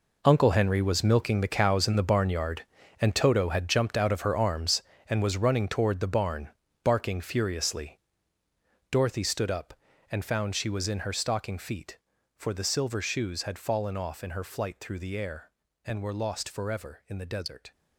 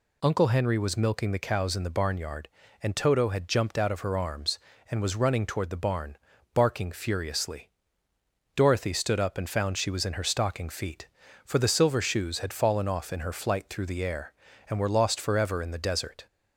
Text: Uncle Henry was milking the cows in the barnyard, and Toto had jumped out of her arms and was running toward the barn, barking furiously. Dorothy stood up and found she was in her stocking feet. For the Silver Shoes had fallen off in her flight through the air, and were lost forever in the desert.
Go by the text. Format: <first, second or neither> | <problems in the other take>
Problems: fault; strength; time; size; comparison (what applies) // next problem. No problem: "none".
second | gets quieter; strong; throughout; 13 dB